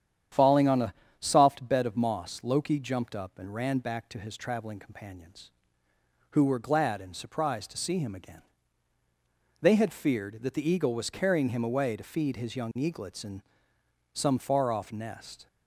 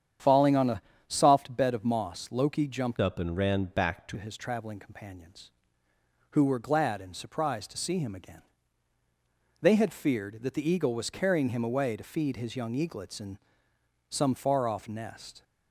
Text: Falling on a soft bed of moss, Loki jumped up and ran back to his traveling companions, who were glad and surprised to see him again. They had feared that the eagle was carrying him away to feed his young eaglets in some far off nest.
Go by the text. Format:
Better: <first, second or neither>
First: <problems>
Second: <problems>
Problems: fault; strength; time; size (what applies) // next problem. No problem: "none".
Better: first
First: starts louder than the rest; strong; until 1.5 s; 9.5 dB // pauses between "a" and "soft"; slight; at 0.9 s; 0.24 s long // pauses between "in" and "some"; noticeable; at 13.4 s; 0.72 s long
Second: starts louder than the rest; strong; until 1.4 s; 9 dB // pauses between "a" and "soft"; slight; at 0.8 s; 0.24 s long // changes voice from "up" to "to"; from 3.0 to 4.1 s; 1.1 s long // pauses between "in" and "some"; noticeable; at 13.3 s; 0.72 s long